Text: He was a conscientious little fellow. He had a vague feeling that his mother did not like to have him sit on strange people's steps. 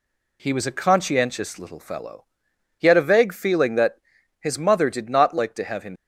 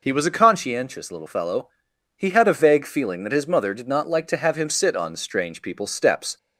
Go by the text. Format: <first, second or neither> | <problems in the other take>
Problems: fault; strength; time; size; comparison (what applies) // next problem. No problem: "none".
second | pauses between "that" and "his"; at 3.9 s; 0.42 s long // stops before "sit on strange people's steps"; at 5.9 s